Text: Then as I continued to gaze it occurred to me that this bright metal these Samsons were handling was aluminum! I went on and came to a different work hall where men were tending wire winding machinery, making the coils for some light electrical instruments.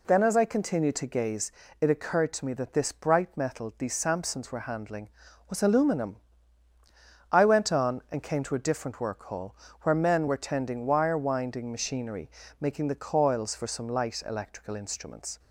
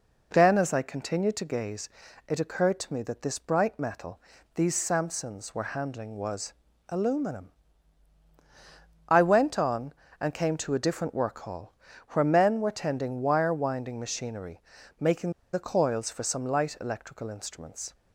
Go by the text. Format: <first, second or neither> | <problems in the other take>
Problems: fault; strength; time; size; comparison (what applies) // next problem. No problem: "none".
first | pauses between "gaze" and "it"; at 1.8 s; 0.38 s long; slight in the first // pauses between "metal" and "these"; slight; at 4.1 s; 0.36 s long // pauses between "was" and "aluminum"; slight; at 6.5 s; 0.34 s long // pauses between "hall" and "where"; at 11.7 s; 0.38 s long; slight in the first // pauses between "making" and "the"; slight; at 15.3 s; 0.21 s long